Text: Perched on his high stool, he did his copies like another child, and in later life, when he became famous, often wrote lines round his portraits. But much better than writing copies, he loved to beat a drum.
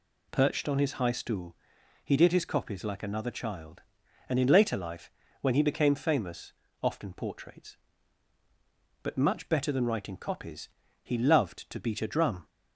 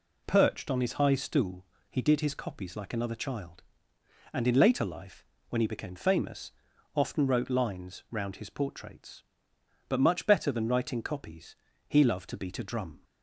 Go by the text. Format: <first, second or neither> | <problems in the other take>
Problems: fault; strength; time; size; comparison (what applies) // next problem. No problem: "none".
second | skips "wrote lines round his"; at 7.1 s